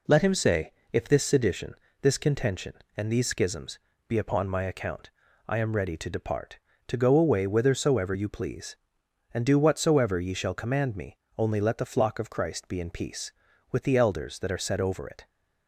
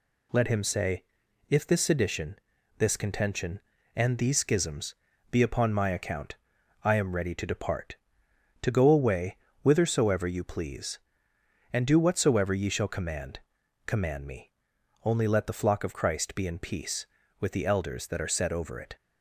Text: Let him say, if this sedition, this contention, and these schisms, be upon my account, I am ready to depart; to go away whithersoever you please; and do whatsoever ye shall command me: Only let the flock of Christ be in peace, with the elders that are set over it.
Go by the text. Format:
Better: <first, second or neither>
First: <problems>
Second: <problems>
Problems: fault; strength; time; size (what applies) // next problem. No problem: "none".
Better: first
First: none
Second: pauses between "away" and "whithersoever"; slight; at 9.3 s; 0.24 s long // says "command" twice; at 13.8 s